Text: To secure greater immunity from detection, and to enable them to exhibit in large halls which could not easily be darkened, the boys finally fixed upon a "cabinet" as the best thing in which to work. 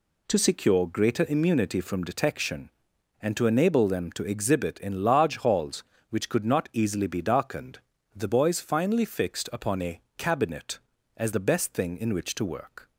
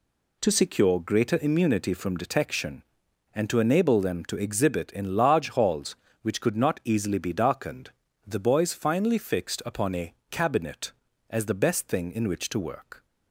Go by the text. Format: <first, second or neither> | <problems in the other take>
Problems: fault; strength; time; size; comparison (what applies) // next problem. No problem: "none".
neither | pauses between "a" and "cabinet"; slight; the same in both